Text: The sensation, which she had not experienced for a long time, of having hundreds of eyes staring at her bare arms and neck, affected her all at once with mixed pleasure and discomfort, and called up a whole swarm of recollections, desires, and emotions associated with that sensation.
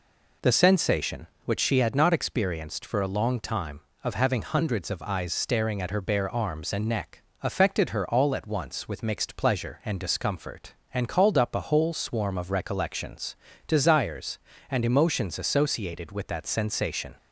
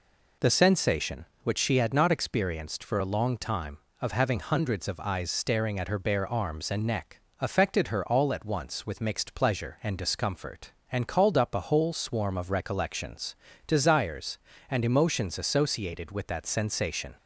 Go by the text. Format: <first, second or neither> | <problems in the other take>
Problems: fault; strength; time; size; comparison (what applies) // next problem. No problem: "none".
neither | none